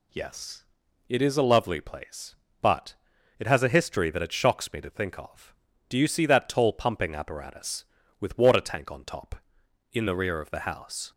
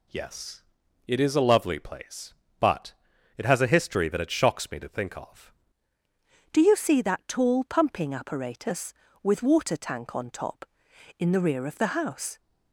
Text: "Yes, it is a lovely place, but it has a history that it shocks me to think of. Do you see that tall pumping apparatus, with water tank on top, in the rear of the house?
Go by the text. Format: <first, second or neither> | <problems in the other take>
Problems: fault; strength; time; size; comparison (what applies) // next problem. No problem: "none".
first | pauses between "but" and "it"; at 2.9 s; 0.42 s long; also in the first // changes voice at "Do"; from 6.5 s on; 5.8 s long